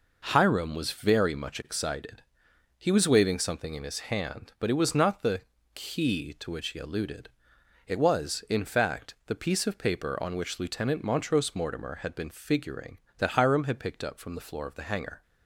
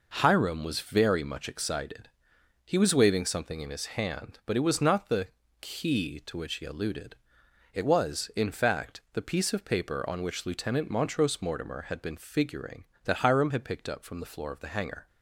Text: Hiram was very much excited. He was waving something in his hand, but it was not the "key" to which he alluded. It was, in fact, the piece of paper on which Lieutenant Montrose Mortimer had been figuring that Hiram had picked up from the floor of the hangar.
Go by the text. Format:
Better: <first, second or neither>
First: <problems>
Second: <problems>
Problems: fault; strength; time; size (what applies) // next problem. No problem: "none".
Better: neither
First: pauses between "the" and "key"; slight; at 5.4 s; 0.34 s long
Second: pauses between "the" and "key"; slight; at 5.2 s; 0.34 s long